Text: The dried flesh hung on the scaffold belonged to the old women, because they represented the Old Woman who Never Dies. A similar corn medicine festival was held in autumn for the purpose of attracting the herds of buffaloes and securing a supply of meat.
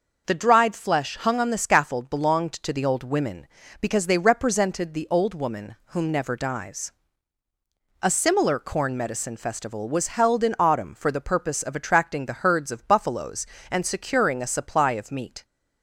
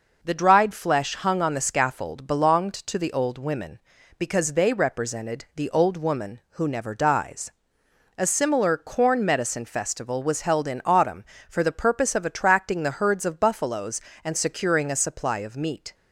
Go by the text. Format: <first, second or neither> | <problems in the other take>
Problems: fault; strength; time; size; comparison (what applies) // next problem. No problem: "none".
second | says "whom" for "who"; at 5.8 s